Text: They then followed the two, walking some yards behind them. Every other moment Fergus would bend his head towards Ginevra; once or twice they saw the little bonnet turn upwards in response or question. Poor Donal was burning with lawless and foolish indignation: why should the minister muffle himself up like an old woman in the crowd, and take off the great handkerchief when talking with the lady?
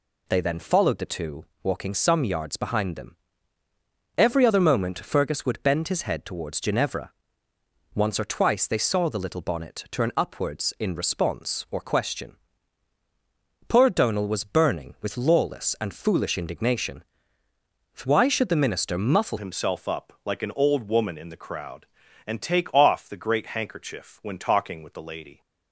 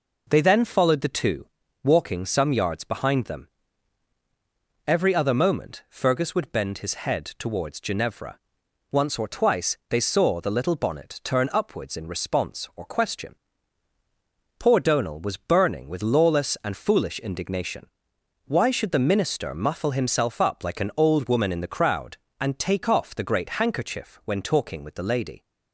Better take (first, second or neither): second